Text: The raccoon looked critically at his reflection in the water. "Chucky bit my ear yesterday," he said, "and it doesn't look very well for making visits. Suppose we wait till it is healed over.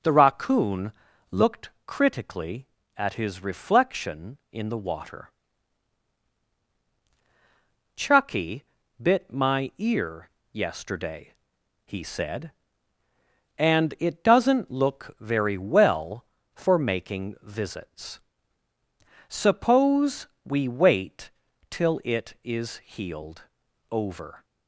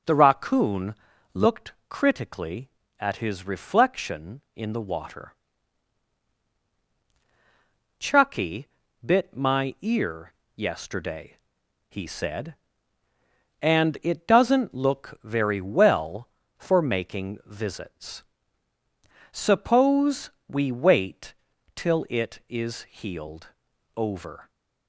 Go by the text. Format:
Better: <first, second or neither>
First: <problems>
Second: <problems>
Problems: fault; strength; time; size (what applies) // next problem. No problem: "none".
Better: neither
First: pauses between "raccoon" and "looked"; slight; at 0.9 s; 0.36 s long // pauses between "Chucky" and "bit"; at 8.6 s; 0.40 s long // pauses between "ear" and "yesterday"; slight; at 10.3 s; 0.22 s long // pauses between "Suppose" and "we"; slight; at 20.2 s; 0.16 s long // pauses between "wait" and "till"; at 21.3 s; 0.40 s long // pauses between "healed" and "over"; noticeable; at 23.4 s; 0.48 s long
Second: pauses between "raccoon" and "looked"; slight; at 0.9 s; 0.36 s long // pauses between "Chucky" and "bit"; at 8.6 s; 0.40 s long // pauses between "ear" and "yesterday"; slight; at 10.3 s; 0.22 s long // pauses between "Suppose" and "we"; slight; at 20.3 s; 0.16 s long // pauses between "wait" and "till"; at 21.3 s; 0.41 s long // pauses between "healed" and "over"; noticeable; at 23.4 s; 0.48 s long